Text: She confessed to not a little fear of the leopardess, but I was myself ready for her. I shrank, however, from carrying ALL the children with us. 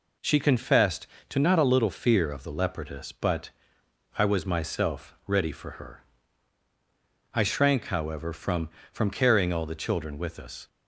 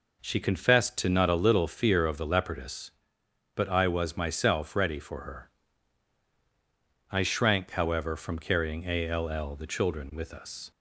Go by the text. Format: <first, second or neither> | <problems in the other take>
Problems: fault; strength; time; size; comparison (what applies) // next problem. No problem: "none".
second | pauses between "but" and "I"; noticeable; at 3.5 s; 0.66 s long // says "from" twice; at 8.9 s